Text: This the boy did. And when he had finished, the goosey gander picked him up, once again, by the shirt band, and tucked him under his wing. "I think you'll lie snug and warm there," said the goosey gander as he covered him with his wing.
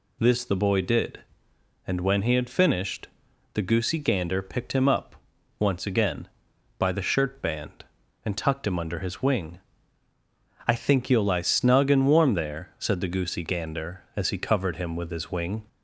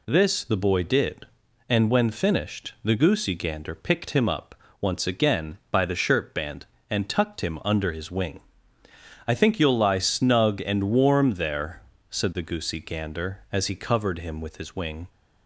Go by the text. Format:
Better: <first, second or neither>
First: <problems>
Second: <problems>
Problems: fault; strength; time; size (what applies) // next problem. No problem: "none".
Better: first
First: none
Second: skips "he had"; at 2.1 s